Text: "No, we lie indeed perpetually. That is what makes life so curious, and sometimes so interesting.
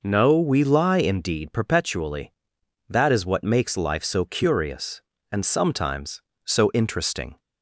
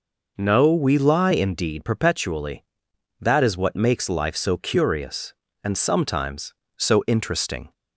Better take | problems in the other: neither | none

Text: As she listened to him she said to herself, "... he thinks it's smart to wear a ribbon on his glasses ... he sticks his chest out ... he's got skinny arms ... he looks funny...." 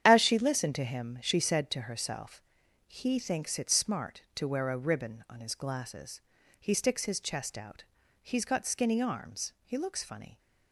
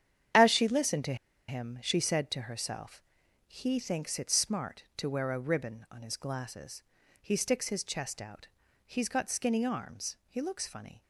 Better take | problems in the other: first | starts louder than the rest; strong; until 1.7 s; 9 dB; strong in the first // pauses between "to" and "him"; slight; at 1.1 s; 0.33 s long

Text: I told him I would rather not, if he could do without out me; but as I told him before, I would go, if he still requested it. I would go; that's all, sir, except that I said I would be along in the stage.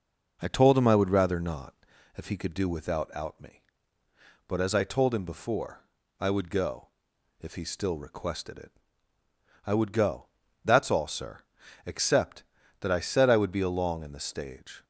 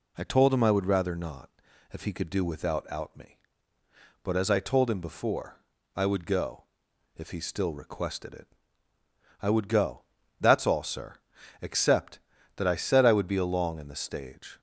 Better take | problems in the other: second | starts louder than the rest; noticeable; until 2.1 s; 5 dB

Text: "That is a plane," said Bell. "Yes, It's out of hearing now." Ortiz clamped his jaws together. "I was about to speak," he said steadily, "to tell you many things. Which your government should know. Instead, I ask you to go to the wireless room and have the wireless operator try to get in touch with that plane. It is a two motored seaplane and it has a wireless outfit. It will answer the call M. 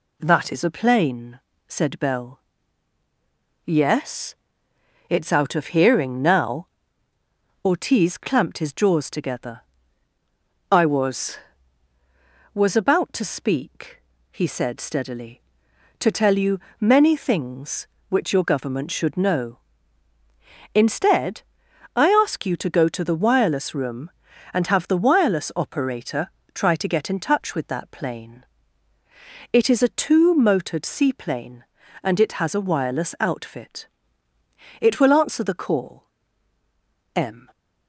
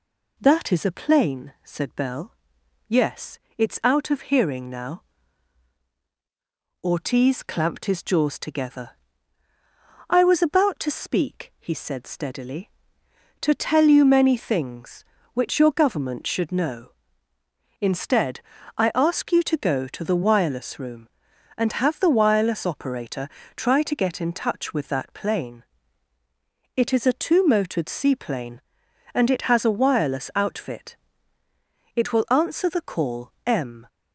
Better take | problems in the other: second | says "was" twice; at 12.5 s // pauses between "you" and "many"; slight; at 16.5 s; 0.22 s long // pauses between "operator" and "try"; slight; at 26.2 s; 0.24 s long; slight in the second // pauses between "call" and "M"; at 36.0 s; 1.1 s long

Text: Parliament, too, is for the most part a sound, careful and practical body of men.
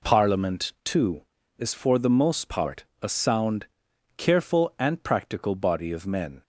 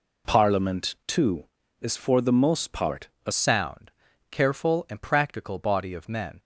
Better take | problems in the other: first | pauses between "part" and "a"; slight; at 3.0 s; 0.18 s long; slight in the first // changes voice at "sound"; from 3.3 s on; 3.0 s long

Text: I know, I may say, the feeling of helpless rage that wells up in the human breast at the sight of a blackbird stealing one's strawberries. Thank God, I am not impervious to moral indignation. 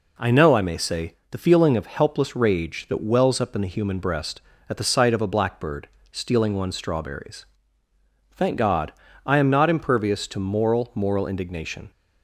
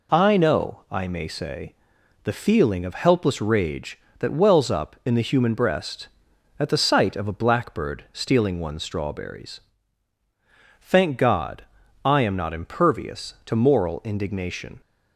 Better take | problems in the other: second | pauses between "blackbird" and "stealing"; slight; at 5.8 s; 0.24 s long // says "moral" twice; at 10.9 s

